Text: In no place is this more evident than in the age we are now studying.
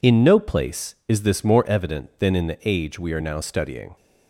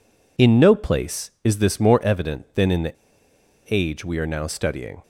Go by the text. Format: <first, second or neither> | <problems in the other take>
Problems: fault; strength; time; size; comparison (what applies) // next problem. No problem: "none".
first | pauses between "the" and "age"; noticeable; at 2.9 s; 0.75 s long